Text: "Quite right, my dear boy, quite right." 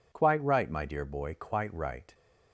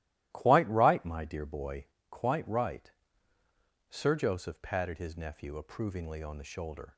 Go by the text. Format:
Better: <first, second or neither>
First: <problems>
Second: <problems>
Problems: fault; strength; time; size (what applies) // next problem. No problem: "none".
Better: first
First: none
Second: starts louder than the rest; strong; until 1.3 s; 15 dB // goes on to say "Sir Joseph patted his nephew approvingly on the shoulder"; strong; from 3.8 s on; 3.0 s long